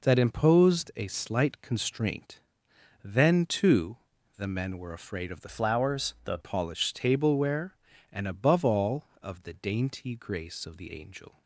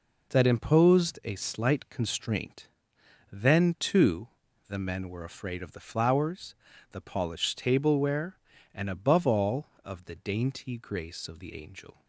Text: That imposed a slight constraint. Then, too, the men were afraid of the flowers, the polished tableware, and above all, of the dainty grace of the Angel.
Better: second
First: changes voice from "flowers" to "the"; from 5.4 to 6.3 s; 0.9 s long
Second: none

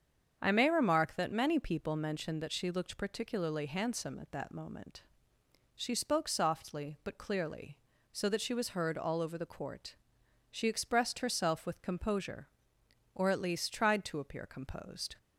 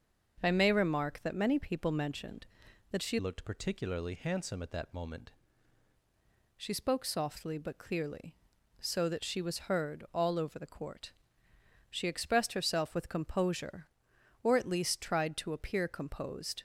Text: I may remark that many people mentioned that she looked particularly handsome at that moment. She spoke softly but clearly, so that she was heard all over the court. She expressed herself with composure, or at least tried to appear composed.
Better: first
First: starts louder than the rest; strong; until 1.4 s; 7.5 dB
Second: starts louder than the rest; until 1.4 s; 6.5 dB // changes voice from "looked" to "moment"; from 3.1 to 5.3 s; 2.2 s long

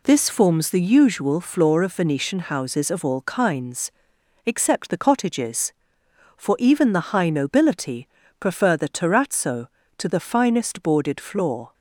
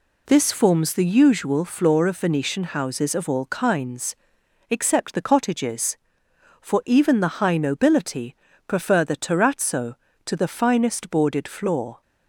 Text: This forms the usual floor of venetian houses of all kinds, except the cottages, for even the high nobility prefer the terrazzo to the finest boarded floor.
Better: neither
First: pauses between "nobility" and "prefer"; slight; at 8.0 s; 0.32 s long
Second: pauses between "nobility" and "prefer"; slight; at 8.3 s; 0.32 s long

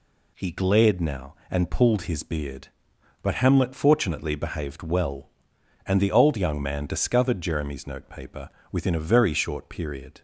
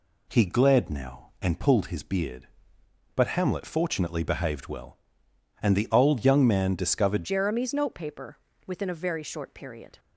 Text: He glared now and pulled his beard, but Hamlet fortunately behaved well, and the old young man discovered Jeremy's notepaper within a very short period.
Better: first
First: pauses between "notepaper" and "within"; slight; at 8.4 s; 0.22 s long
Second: changes voice at "Jeremy's"; from 7.2 s on; 2.7 s long // pauses between "notepaper" and "within"; slight; at 8.3 s; 0.28 s long

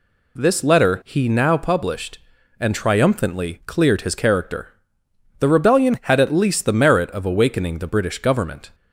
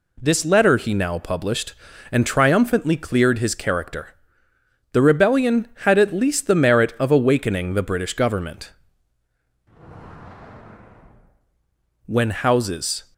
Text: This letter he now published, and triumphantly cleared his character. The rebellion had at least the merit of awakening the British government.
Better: first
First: none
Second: goes on to say "When houses"; noticeable; from 12.0 s on; 1.0 s long

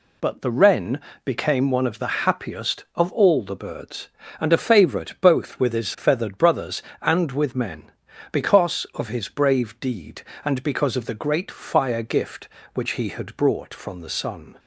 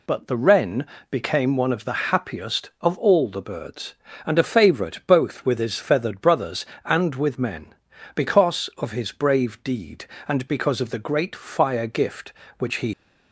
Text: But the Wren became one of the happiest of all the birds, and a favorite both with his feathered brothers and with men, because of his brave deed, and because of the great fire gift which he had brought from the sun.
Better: first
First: pauses between "Wren" and "became"; slight; at 1.0 s; 0.26 s long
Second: pauses between "Wren" and "became"; slight; at 0.8 s; 0.26 s long // stops before "had brought from the sun"; at 12.9 s

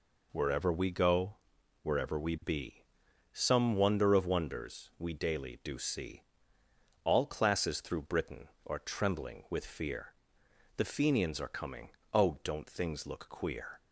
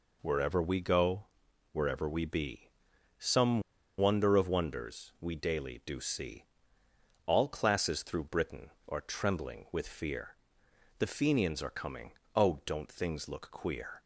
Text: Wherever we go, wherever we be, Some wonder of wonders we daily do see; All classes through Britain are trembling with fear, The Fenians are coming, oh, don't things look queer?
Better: first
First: none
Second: pauses between "Some" and "wonder"; at 3.6 s; 0.36 s long

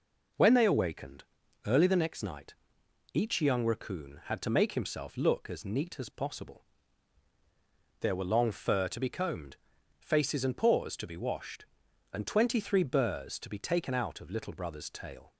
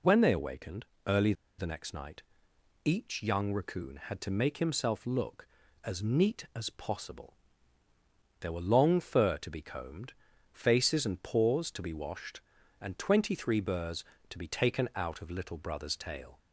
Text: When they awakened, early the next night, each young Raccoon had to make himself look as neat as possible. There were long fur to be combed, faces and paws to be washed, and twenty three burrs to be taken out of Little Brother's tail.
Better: first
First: none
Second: pauses between "early" and "the"; slight; at 1.3 s; 0.25 s long

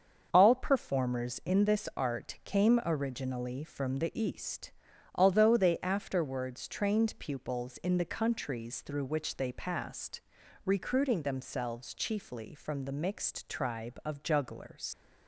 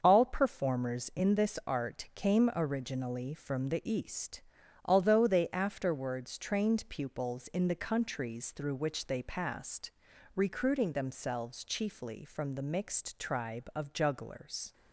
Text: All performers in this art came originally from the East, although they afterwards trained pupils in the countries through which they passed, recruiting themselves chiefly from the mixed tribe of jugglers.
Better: second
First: starts louder than the rest; until 1.3 s; 7 dB // leaves "jugglers" unfinished; at 14.9 s; 95 ms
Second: starts louder than the rest; until 1.0 s; 7 dB

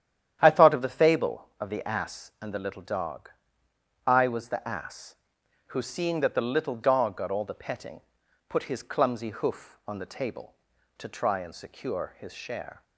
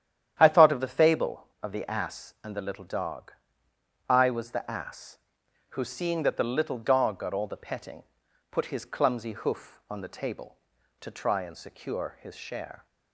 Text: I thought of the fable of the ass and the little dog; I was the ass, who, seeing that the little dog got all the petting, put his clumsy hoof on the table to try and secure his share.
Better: neither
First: starts louder than the rest; strong; until 1.4 s; 10 dB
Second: starts louder than the rest; strong; until 1.4 s; 10 dB

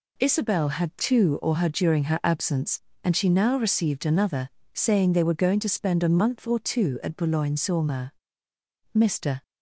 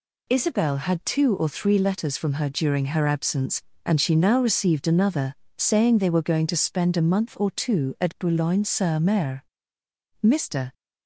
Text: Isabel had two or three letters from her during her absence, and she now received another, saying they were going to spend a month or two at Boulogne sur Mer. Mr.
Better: second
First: skips "three letters from"; at 1.5 s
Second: none

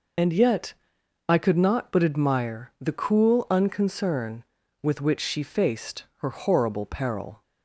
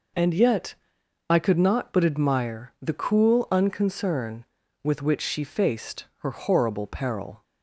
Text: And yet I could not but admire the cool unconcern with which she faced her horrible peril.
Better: second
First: loses the start of "And"; at 0.1 s; 30 ms // pauses between "yet" and "I"; noticeable; at 0.7 s; 0.54 s long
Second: pauses between "yet" and "I"; noticeable; at 0.7 s; 0.54 s long

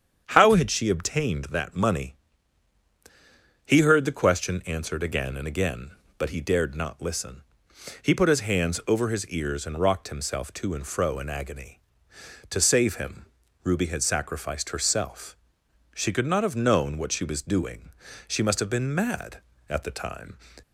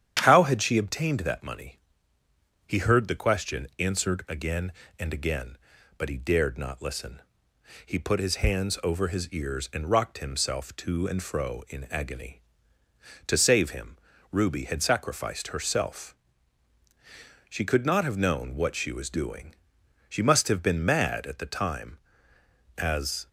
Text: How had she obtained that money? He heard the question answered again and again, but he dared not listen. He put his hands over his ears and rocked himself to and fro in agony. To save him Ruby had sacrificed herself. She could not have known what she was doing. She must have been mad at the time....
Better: first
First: starts louder than the rest; strong; until 1.2 s; 8 dB // pauses between "him" and "Ruby"; at 13.2 s; 0.38 s long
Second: starts louder than the rest; strong; until 1.2 s; 9.5 dB // pauses between "him" and "Ruby"; slight; at 13.9 s; 0.34 s long // goes on to say "As"; from 22.7 s on; 0.52 s long

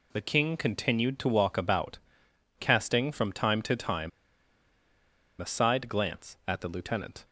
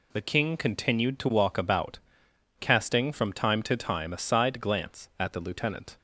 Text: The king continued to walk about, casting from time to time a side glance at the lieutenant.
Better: second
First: pauses between "time" and "a"; strong; at 4.0 s; 1.3 s long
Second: none

